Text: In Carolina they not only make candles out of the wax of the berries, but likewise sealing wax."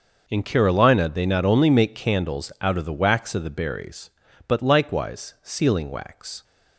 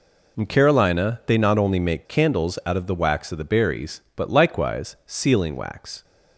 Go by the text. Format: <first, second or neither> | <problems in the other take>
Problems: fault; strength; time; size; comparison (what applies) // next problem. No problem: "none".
neither | none